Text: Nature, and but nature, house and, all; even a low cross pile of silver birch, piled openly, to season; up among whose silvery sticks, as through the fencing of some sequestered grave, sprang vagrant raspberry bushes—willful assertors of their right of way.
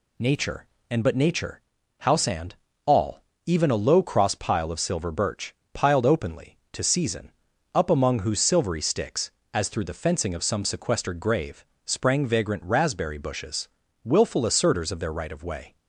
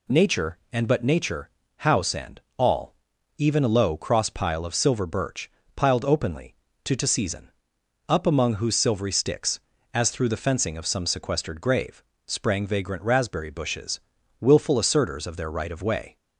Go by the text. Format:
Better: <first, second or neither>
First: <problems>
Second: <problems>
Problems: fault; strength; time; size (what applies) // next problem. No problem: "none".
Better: first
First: none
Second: says "to" twice; at 6.9 s